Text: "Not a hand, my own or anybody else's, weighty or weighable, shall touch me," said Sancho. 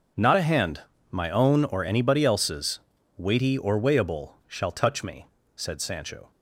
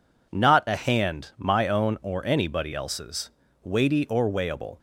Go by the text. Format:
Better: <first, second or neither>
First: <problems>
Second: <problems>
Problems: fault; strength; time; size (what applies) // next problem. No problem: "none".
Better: first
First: none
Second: stops before "shall touch me said Sancho"; at 4.7 s